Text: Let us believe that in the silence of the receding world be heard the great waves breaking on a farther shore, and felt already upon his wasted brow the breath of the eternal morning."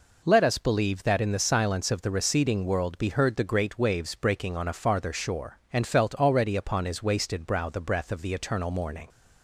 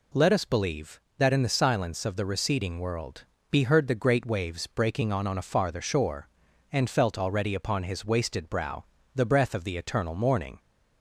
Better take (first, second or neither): first